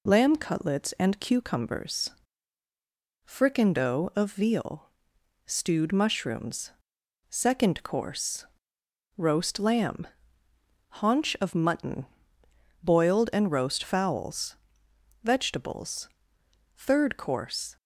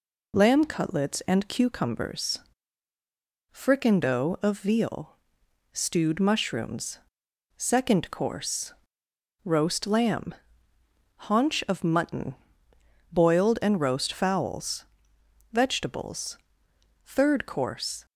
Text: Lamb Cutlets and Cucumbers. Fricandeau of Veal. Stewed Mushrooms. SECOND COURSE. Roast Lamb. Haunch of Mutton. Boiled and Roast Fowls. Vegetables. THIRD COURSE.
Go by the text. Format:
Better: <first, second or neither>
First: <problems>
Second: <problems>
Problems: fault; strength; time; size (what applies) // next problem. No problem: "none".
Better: neither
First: none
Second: none